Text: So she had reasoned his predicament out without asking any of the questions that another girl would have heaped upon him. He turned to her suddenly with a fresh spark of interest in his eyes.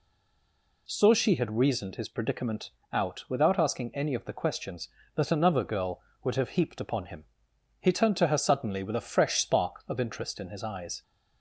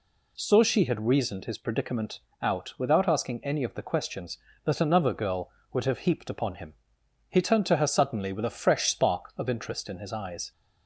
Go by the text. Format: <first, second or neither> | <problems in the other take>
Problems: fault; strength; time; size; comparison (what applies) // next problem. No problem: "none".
second | stays silent before the first word; slight; until 0.8 s; 0.8 s long // pauses between "predicament" and "out"; slight; at 2.7 s; 0.22 s long; slight in the second